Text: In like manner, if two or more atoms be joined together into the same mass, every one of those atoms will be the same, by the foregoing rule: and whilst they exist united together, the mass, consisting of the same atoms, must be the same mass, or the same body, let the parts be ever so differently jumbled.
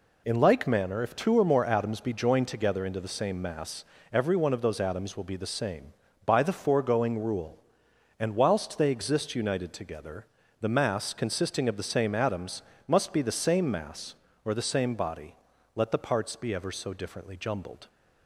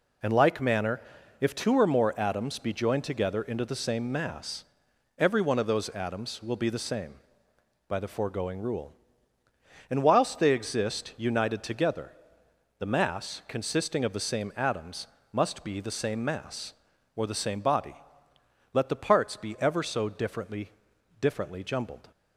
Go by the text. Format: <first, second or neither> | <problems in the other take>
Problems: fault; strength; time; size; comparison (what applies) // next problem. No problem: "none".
first | says "differently" twice; at 21.1 s